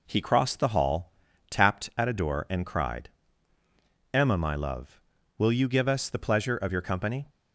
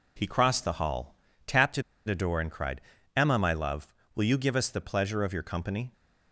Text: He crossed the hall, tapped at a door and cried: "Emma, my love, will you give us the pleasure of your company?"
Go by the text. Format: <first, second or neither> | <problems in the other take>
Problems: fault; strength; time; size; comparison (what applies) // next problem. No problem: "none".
first | pauses between "at" and "a"; slight; at 1.8 s; 0.25 s long